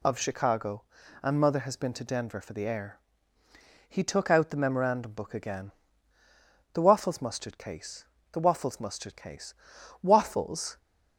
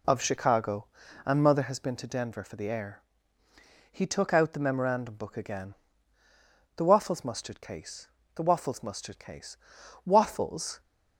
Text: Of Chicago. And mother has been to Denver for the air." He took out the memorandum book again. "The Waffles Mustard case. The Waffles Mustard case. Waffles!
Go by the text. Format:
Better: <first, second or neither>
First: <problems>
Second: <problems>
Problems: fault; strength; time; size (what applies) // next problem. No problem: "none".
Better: first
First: none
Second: starts louder than the rest; slight; until 1.8 s; 2.5 dB